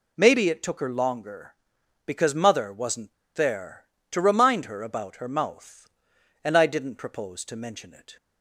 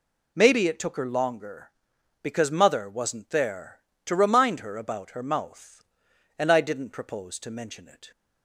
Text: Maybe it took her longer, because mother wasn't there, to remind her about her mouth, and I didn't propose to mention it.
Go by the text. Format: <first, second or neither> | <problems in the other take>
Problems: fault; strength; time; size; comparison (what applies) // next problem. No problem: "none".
second | pauses between "wasn't" and "there"; slight; at 3.1 s; 0.23 s long